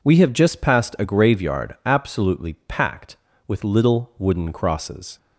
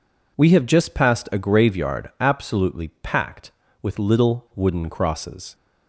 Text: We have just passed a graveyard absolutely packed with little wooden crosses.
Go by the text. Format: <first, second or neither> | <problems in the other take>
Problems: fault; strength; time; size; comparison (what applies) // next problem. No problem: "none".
neither | none